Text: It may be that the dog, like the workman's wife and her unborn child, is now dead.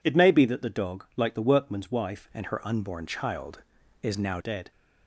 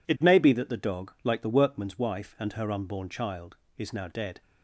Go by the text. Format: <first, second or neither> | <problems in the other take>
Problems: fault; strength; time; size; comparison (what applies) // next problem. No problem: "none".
second | changes voice from "and" to "now"; from 2.3 to 4.3 s; 2.0 s long